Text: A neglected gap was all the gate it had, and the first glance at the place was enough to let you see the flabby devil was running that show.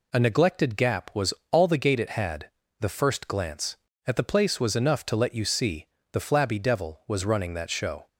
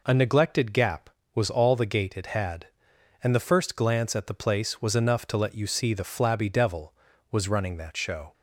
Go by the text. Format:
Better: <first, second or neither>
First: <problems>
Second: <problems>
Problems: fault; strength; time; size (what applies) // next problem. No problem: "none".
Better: second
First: pauses between "was" and "all"; slight; at 1.3 s; 0.18 s long // skips "and"; at 2.6 s // pauses between "see" and "the"; slight; at 5.8 s; 0.28 s long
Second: none